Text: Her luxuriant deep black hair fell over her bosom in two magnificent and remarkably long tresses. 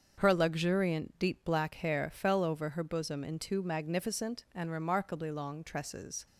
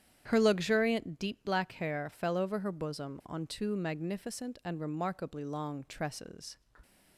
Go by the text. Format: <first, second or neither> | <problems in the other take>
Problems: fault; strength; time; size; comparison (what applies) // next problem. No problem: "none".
first | starts louder than the rest; strong; until 1.2 s; 9.5 dB; also in the first // says "on" for "in"; at 3.2 s